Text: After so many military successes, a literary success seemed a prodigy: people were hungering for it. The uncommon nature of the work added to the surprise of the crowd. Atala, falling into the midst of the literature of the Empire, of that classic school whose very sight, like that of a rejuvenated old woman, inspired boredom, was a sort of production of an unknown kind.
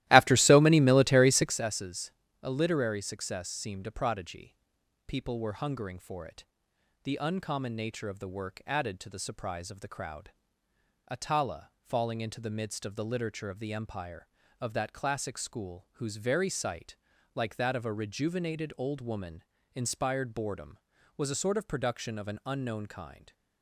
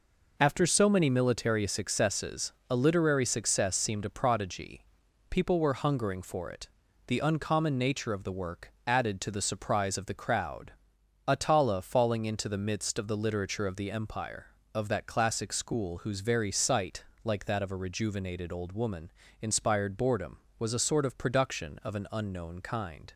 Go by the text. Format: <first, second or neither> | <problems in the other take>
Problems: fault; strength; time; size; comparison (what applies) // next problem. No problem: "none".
second | starts louder than the rest; strong; until 1.6 s; 15.5 dB